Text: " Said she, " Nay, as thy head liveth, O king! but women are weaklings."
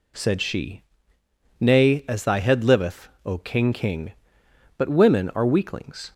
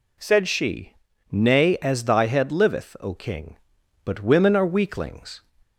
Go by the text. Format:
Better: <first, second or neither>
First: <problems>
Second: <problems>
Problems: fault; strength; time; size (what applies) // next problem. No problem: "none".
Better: second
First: says "king" twice; at 3.7 s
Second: none